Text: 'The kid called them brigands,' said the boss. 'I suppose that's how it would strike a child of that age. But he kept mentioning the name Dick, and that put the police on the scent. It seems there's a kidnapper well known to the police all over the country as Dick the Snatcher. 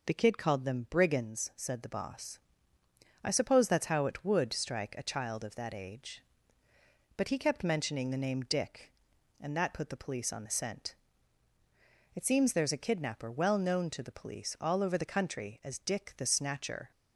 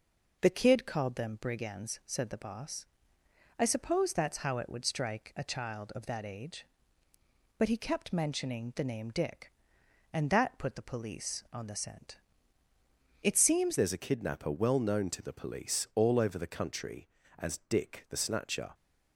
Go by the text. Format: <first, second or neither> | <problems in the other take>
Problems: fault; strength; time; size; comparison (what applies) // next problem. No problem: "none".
first | changes voice at "there's"; from 13.7 s on; 5.0 s long